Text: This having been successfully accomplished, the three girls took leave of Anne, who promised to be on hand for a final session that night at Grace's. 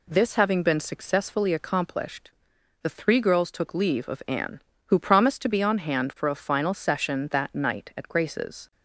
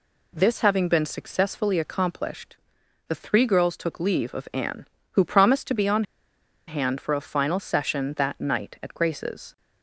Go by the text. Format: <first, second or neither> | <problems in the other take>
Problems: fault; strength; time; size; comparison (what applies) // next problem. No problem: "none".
first | pauses between "on" and "hand"; noticeable; at 6.0 s; 0.65 s long